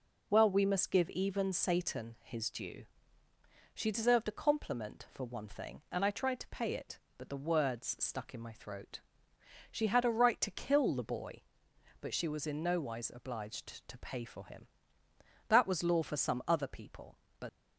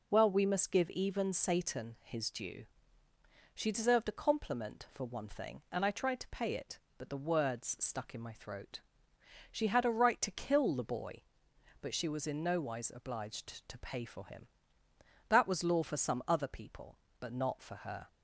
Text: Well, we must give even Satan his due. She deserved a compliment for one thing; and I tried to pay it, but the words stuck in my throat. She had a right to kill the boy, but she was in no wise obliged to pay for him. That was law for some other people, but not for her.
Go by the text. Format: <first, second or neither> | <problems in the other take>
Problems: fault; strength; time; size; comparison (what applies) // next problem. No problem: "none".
second | stops before "not for her"; at 17.4 s